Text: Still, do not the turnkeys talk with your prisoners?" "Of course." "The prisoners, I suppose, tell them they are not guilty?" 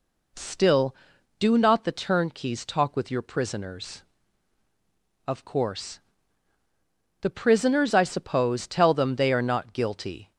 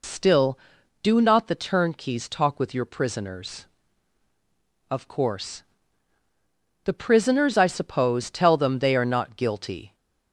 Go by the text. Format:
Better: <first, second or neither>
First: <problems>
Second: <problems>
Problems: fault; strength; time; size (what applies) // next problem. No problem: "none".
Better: first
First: none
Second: loses the start of "Still"; at 0.0 s; 45 ms